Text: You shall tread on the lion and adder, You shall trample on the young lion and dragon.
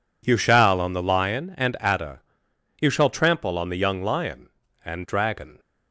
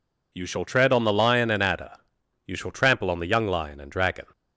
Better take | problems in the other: second | skips "tread"; at 0.7 s

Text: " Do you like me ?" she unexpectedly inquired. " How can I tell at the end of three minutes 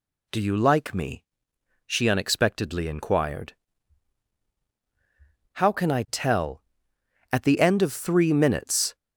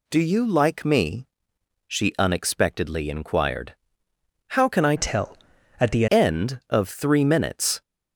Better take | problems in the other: first | changes voice from "tell" to "the"; from 4.9 to 6.0 s; 1.1 s long

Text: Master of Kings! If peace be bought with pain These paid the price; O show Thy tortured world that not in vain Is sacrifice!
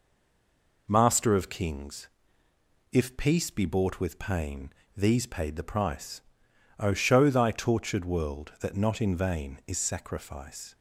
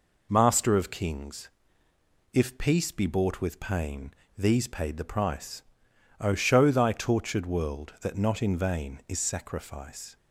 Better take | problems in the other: second | stays silent before the first word; slight; until 0.8 s; 0.8 s long // pauses between "pain" and "These"; slight; at 4.7 s; 0.24 s long; slight in the second

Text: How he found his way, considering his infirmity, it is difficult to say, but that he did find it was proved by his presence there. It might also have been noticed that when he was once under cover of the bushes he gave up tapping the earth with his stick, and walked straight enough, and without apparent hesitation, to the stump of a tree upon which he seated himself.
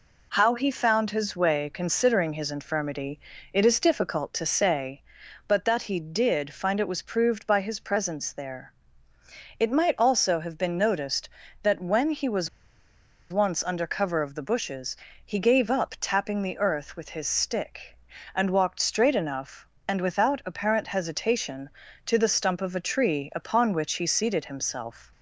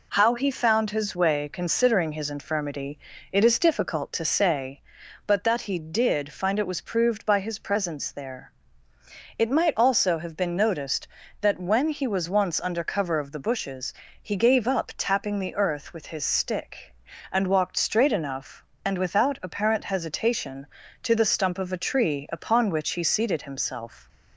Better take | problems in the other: second | pauses between "was" and "once"; noticeable; at 12.4 s; 0.84 s long // pauses between "bushes" and "he"; slight; at 14.9 s; 0.30 s long; slight in the second

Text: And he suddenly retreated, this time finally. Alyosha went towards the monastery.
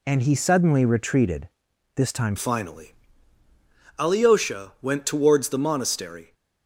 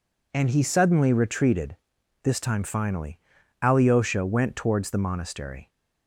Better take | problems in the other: second | changes voice at "finally"; from 2.3 s on; 4.0 s long

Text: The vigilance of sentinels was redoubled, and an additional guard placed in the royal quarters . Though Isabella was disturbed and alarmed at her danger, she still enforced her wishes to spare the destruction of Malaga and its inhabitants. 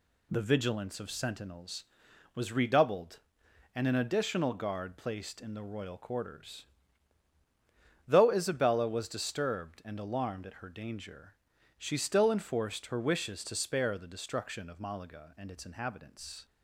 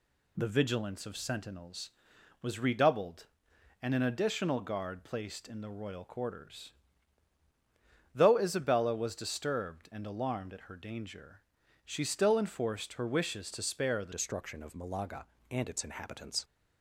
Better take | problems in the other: first | changes voice at "destruction"; from 14.1 s on; 2.3 s long

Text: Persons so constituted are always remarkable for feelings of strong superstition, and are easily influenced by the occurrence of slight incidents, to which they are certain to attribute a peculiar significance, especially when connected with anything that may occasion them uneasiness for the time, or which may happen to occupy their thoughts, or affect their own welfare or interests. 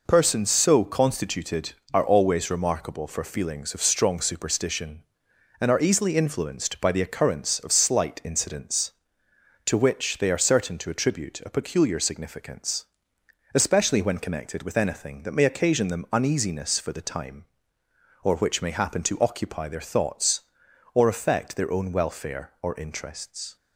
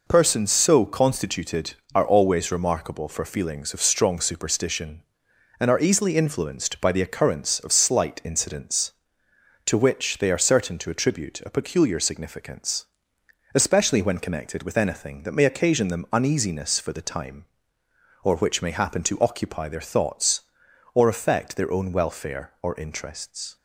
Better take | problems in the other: neither | none

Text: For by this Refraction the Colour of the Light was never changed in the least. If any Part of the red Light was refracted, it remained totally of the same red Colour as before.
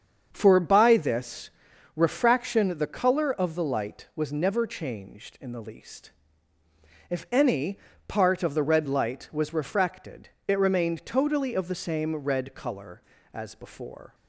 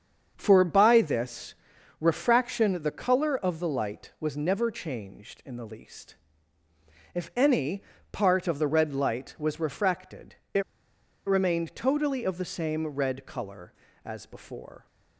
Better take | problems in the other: first | starts louder than the rest; strong; until 1.3 s; 7 dB; strong in the first // pauses between "this" and "Refraction"; at 1.5 s; 0.44 s long; also in the first // pauses between "any" and "Part"; slight; at 7.8 s; 0.30 s long; slight in the first // pauses between "it" and "remained"; noticeable; at 10.6 s; 0.64 s long

